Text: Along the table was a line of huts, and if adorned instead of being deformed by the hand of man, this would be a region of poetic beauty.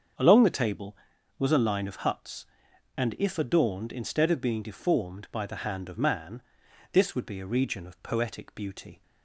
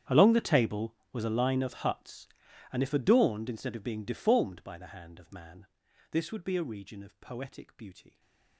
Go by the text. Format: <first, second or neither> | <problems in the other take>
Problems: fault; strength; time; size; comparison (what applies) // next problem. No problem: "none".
first | gets quieter; strong; throughout; 21 dB // starts louder than the rest; strong; until 1.2 s; 9.5 dB; also in the first // stays silent after the last word; slight; from 8.0 s on; 0.5 s long